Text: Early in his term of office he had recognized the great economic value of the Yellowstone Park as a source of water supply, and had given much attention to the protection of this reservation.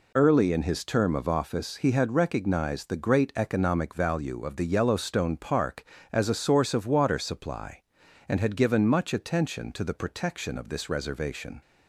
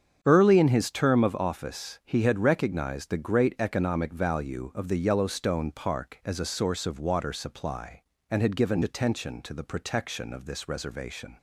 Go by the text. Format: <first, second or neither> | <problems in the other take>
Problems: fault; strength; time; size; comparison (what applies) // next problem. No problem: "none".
first | starts louder than the rest; strong; until 1.2 s; 7.5 dB // skips "much"; at 8.8 s